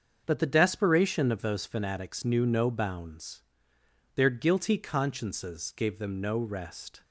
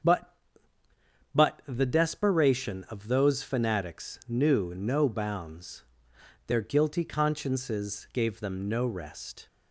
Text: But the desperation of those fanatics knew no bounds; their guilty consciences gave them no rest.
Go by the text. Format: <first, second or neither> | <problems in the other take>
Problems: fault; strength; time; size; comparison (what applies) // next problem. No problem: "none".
first | starts louder than the rest; until 2.1 s; 7 dB; also in the first // says "But" twice; at 1.3 s